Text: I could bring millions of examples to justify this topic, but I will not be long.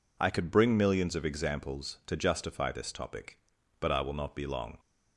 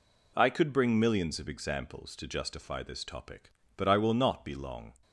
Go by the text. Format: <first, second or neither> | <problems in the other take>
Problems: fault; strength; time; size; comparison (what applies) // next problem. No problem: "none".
neither | none